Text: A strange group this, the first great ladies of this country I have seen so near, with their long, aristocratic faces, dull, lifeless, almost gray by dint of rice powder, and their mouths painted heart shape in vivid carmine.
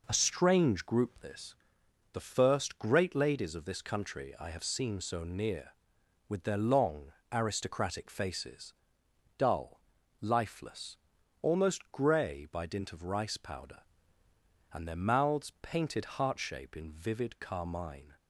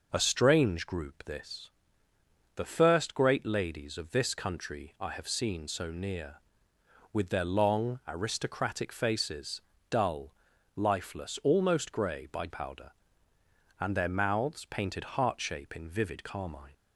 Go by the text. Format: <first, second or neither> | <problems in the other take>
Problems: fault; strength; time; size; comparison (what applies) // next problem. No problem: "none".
first | skips "dint of rice"; at 12.4 s